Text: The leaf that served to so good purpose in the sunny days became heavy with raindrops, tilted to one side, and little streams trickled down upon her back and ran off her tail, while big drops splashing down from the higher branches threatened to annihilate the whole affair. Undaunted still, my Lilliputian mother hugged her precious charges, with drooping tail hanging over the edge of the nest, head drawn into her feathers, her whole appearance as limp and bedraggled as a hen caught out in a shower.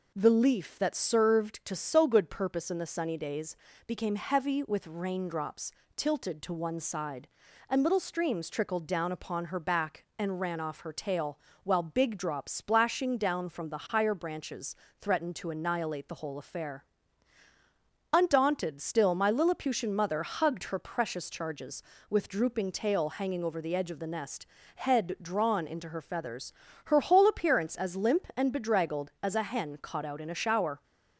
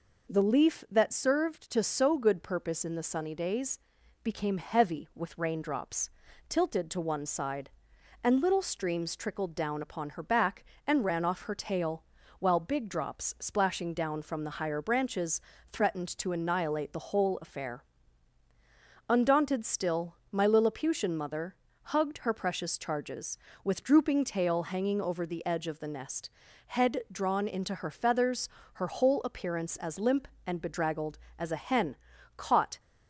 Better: first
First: pauses between "days" and "became"; slight; at 3.5 s; 0.32 s long // pauses between "branches" and "threatened"; slight; at 14.7 s; 0.26 s long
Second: pauses between "days" and "became"; at 3.7 s; 0.44 s long // pauses between "branches" and "threatened"; slight; at 15.3 s; 0.30 s long // pauses between "mother" and "hugged"; slight; at 21.5 s; 0.36 s long // pauses between "hen" and "caught"; at 31.9 s; 0.42 s long // stops before "out in a shower"; at 32.7 s

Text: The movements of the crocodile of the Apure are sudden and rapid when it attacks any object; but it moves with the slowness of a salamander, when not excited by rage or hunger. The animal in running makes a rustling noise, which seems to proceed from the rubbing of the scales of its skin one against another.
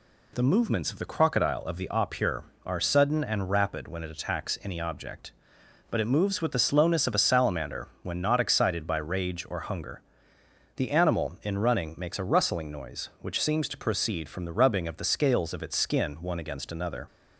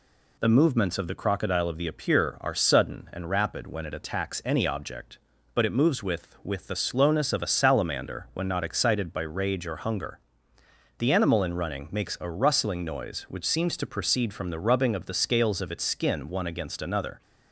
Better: first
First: none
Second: says "with" twice; at 6.4 s

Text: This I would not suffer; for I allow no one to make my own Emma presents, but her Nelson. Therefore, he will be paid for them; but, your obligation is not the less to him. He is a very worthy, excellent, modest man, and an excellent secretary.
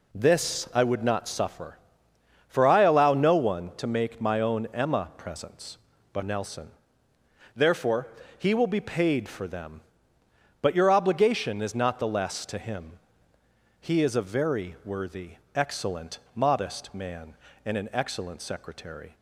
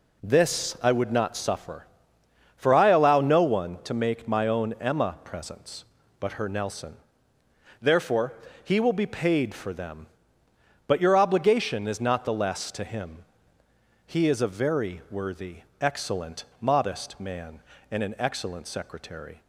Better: second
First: skips "her"; at 6.2 s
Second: none

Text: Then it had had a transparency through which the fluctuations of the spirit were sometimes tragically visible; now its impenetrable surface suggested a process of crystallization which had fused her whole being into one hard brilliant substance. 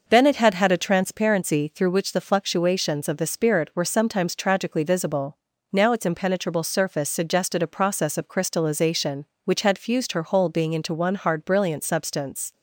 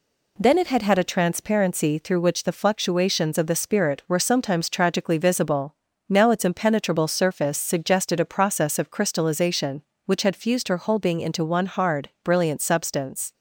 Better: neither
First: none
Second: none

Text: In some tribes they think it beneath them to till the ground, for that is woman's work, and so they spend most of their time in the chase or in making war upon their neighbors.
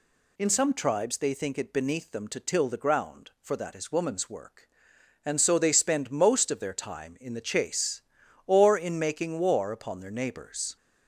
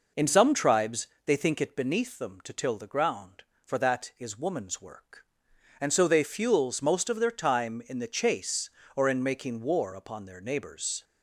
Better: first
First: none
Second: pauses between "tribes" and "they"; slight; at 1.0 s; 0.18 s long // says "fuels" for "spend"; at 6.2 s

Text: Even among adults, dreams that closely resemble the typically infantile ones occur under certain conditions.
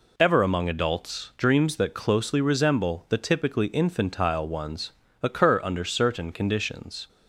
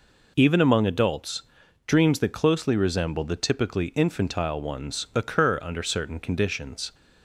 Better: second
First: says "Ever" for "Even"; at 0.1 s // pauses between "ones" and "occur"; slight; at 4.9 s; 0.30 s long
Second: none

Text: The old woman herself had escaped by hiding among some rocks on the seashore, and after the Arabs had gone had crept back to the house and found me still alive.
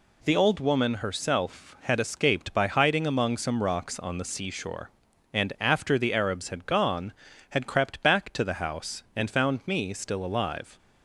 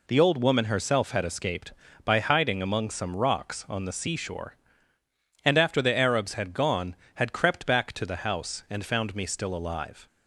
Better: neither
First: none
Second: none

